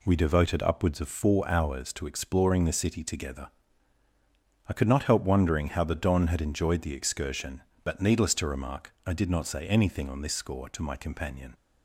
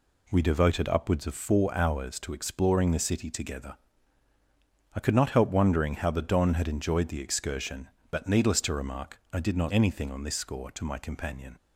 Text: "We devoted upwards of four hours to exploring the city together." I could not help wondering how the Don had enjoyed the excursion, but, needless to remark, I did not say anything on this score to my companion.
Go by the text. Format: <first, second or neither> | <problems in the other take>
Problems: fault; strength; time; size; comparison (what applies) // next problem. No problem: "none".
first | skips "say"; at 9.7 s